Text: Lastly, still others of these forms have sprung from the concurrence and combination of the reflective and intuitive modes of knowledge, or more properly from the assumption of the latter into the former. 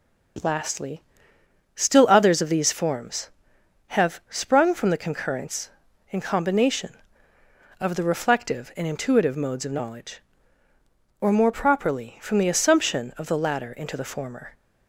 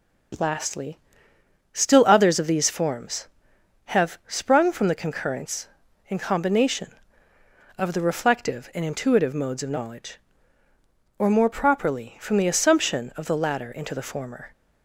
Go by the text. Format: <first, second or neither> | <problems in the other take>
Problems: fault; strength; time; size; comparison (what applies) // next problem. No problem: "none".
neither | starts louder than the rest; the same in both